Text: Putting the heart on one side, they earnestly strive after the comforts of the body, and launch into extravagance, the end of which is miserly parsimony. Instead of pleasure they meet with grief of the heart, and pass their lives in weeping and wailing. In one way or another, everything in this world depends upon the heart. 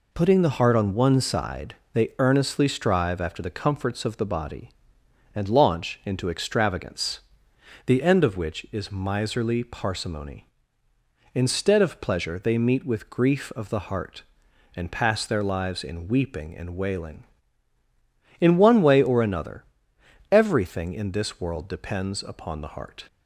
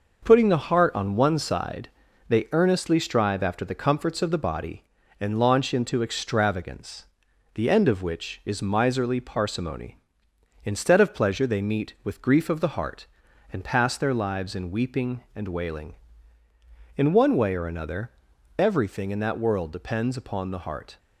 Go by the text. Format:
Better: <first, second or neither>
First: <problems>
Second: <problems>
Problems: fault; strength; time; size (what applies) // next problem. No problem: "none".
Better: first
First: none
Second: says "that" for "this"; at 19.1 s